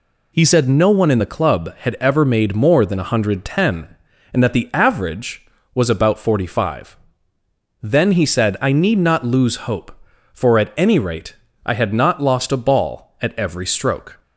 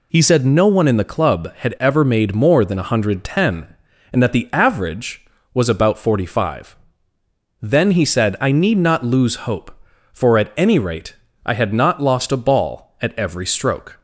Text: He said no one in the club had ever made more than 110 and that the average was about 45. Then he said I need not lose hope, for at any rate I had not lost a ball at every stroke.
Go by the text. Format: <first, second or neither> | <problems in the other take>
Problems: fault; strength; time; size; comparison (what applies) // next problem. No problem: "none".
neither | pauses between "rate" and "I"; slight; the same in both